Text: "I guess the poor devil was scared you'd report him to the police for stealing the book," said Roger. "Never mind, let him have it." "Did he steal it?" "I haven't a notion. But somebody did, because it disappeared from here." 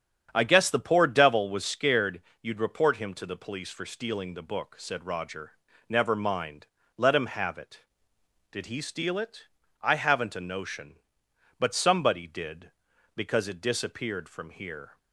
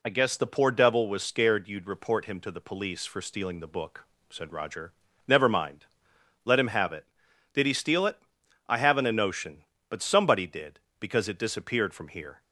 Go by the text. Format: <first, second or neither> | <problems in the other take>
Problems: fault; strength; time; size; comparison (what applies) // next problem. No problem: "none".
second | starts louder than the rest; strong; until 1.3 s; 8 dB // pauses between "scared" and "you'd"; slight; at 2.2 s; 0.18 s long